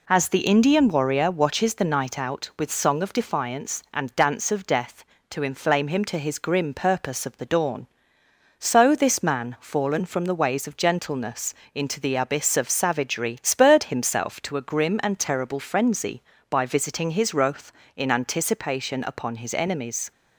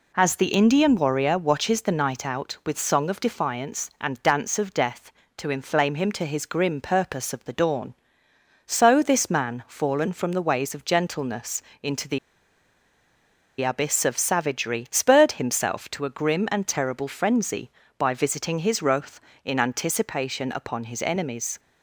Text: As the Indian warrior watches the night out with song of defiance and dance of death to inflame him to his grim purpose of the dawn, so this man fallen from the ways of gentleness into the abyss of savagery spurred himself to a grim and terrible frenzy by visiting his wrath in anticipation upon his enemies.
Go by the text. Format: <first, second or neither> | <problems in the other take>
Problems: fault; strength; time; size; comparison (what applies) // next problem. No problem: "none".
first | pauses between "gentleness" and "into"; slight; at 11.6 s; 0.18 s long; slight in the first // pauses between "the" and "abyss"; strong; at 12.1 s; 1.4 s long